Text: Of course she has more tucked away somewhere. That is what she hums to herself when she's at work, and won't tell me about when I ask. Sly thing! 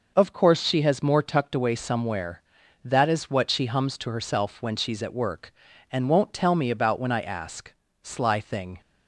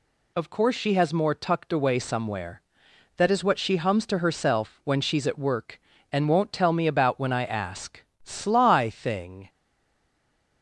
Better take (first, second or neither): first